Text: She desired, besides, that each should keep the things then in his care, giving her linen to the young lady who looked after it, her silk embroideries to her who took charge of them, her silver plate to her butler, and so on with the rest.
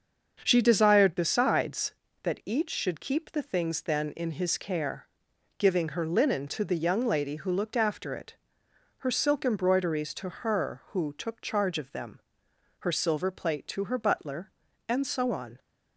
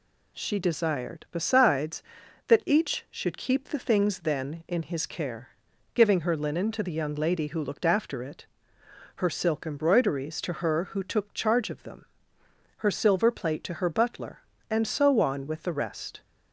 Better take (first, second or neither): second